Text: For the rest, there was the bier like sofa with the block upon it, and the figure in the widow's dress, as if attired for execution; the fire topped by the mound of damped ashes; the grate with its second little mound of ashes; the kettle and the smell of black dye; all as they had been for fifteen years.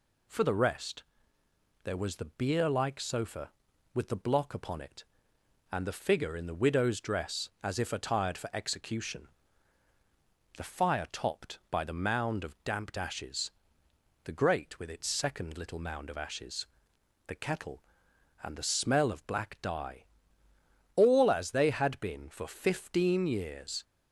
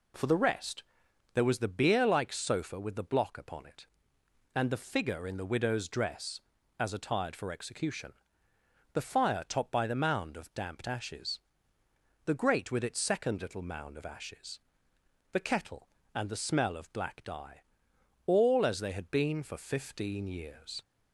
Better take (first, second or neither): first